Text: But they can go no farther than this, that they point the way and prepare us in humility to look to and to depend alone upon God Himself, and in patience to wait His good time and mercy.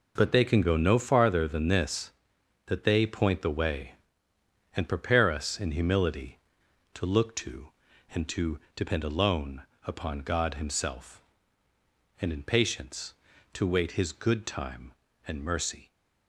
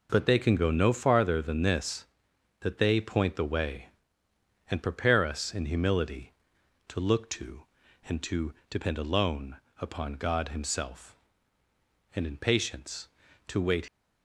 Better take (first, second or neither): first